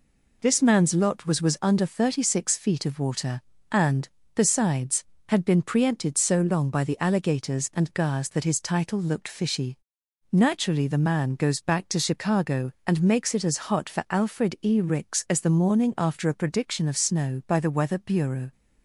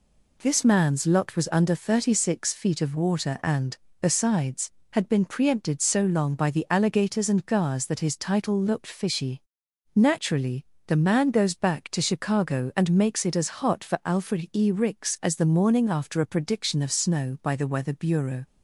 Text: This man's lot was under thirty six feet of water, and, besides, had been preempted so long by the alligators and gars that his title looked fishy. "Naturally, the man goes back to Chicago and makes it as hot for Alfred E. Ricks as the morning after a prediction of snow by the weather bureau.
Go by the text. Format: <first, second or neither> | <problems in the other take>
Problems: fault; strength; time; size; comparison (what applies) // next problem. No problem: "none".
second | says "was" twice; at 1.4 s